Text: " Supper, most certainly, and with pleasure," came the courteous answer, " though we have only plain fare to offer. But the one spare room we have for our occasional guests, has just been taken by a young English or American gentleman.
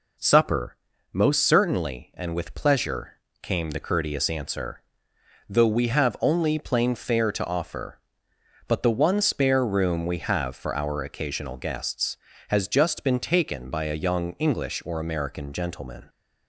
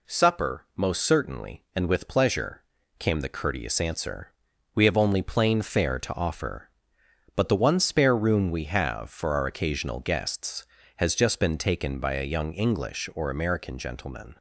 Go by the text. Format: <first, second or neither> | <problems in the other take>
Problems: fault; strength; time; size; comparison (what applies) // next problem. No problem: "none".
first | skips "though"; at 4.7 s